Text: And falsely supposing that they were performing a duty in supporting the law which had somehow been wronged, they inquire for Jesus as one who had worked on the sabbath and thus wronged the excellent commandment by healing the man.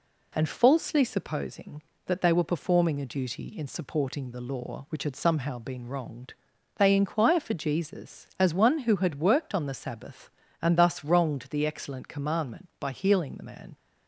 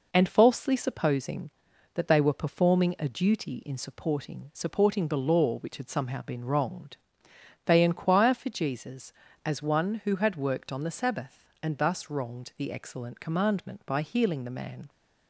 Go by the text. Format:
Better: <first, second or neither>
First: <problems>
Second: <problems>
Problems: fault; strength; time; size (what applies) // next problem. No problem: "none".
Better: first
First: none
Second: says "supporting" twice; at 4.5 s